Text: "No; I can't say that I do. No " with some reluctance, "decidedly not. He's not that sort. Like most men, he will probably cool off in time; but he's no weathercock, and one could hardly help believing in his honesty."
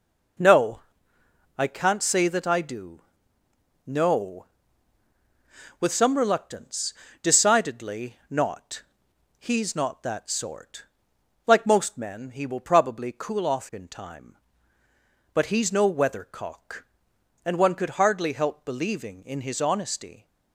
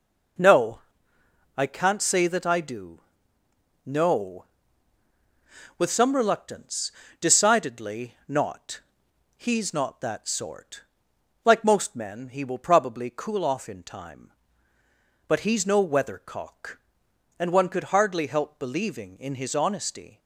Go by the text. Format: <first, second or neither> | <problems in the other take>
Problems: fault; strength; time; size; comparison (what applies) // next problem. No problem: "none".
neither | none